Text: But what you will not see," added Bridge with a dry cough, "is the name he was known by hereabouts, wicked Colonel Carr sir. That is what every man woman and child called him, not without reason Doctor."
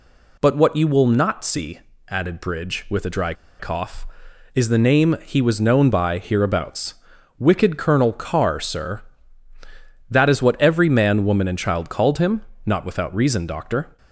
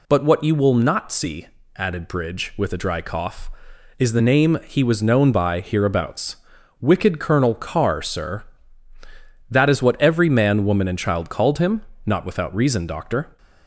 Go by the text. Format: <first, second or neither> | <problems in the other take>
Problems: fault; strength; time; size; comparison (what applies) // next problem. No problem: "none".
second | pauses between "dry" and "cough"; slight; at 3.3 s; 0.25 s long